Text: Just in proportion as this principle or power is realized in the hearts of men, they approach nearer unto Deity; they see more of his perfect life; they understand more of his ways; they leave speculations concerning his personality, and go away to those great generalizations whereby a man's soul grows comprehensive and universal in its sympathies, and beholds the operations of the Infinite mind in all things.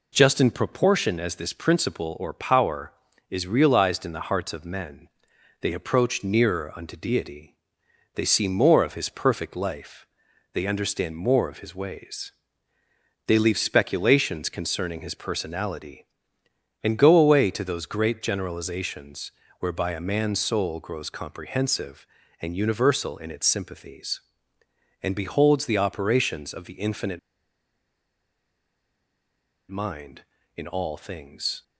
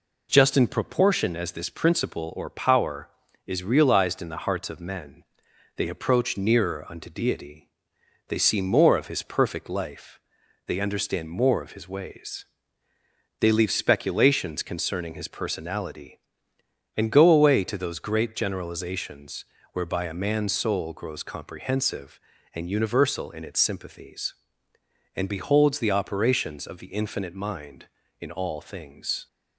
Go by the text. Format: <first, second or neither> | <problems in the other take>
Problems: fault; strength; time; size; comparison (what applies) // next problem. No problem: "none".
second | pauses between "generalizations" and "whereby"; slight; at 19.3 s; 0.26 s long; slight in the second // pauses between "Infinite" and "mind"; strong; at 27.1 s; 2.5 s long